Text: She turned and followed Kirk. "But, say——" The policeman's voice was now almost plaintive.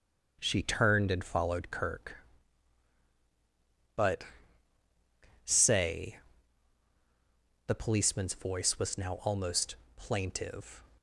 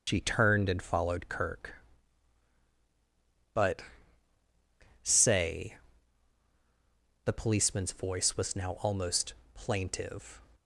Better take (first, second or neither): first